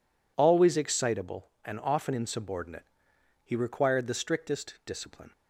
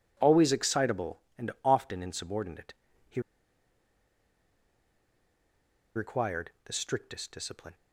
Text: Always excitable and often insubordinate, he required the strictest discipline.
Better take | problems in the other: first | pauses between "he" and "required"; strong; at 3.2 s; 2.7 s long

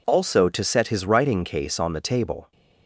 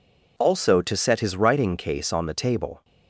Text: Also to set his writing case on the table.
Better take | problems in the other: neither | none

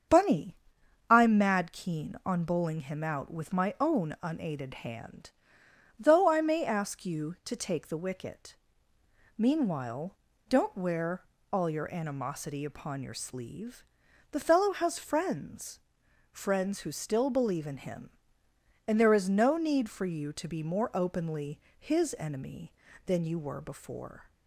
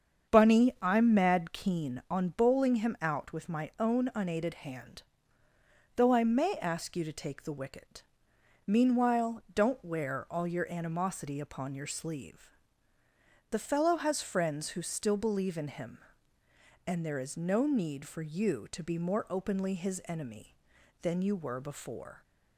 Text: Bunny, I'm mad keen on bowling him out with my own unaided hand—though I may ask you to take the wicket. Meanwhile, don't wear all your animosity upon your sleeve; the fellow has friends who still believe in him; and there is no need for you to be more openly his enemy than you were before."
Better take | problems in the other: second | starts louder than the rest; strong; until 1.6 s; 7.5 dB; strong in the second // pauses between "wear" and "all"; slight; at 11.2 s; 0.28 s long // says "friends" twice; at 16.3 s // pauses between "openly" and "his"; slight; at 21.5 s; 0.18 s long

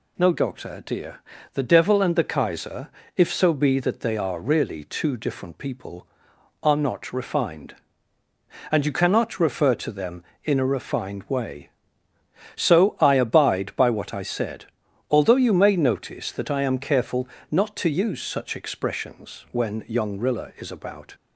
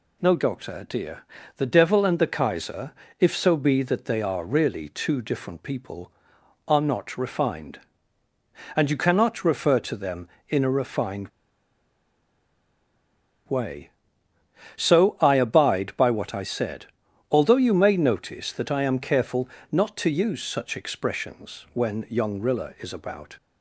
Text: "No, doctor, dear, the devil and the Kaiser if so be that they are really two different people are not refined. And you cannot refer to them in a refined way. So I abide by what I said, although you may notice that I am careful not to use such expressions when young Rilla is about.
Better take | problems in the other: first | pauses between "Kaiser" and "if"; slight; at 2.9 s; 0.30 s long; slight in the first // pauses between "refined" and "way"; strong; at 11.2 s; 2.1 s long // pauses between "careful" and "not"; slight; at 19.4 s; 0.22 s long; slight in the first

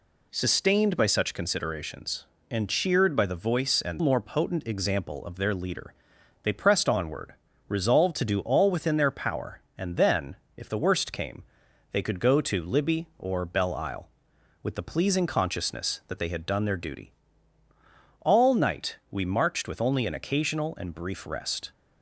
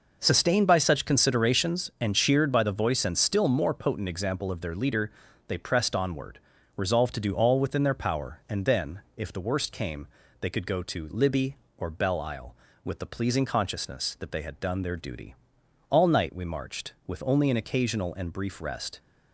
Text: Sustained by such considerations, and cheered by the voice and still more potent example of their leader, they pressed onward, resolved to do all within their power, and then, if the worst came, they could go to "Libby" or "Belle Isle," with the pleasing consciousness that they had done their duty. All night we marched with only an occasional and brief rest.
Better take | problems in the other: second | skips "still"; at 4.0 s

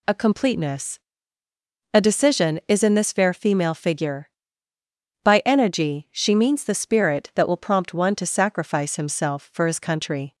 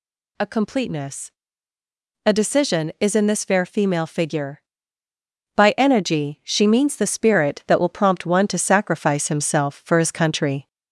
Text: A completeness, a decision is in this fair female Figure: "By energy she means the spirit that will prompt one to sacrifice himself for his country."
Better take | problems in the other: first | gets louder; slight; throughout; 2.5 dB

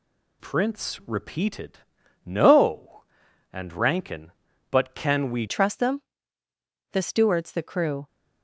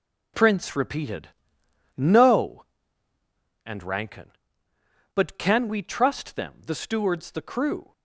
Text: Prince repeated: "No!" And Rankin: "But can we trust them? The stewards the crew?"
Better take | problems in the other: second | changes voice at "trust"; from 5.4 s on; 2.6 s long

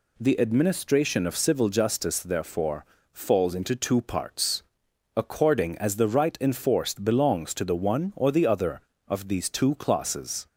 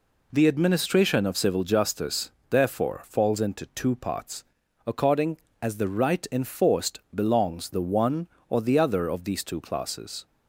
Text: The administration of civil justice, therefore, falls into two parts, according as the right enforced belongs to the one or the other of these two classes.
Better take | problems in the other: first | skips "to"; at 7.6 s

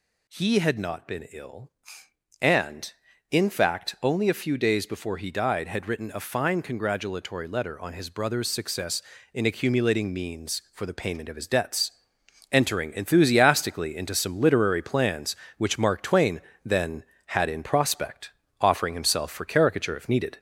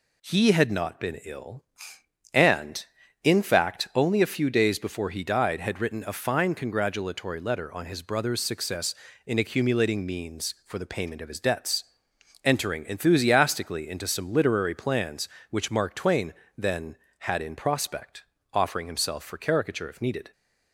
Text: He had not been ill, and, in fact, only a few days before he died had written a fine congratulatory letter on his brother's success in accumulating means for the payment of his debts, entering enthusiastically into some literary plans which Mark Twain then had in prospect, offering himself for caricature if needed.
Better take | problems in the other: second | gets louder; slight; throughout; 3 dB // pauses between "Twain" and "then"; slight; at 16.4 s; 0.24 s long; slight in the second

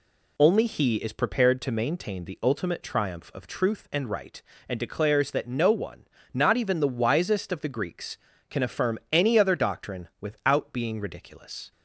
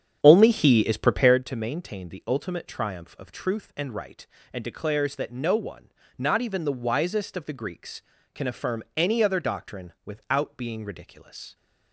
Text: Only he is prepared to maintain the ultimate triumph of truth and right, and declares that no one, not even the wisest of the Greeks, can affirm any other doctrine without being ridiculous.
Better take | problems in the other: first | starts louder than the rest; strong; until 1.4 s; 8.5 dB

